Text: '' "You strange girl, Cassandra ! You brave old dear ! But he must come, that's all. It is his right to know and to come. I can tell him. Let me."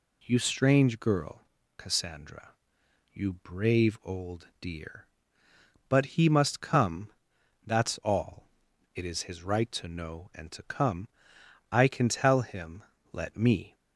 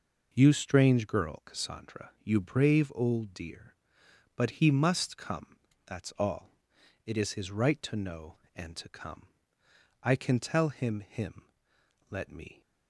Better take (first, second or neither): first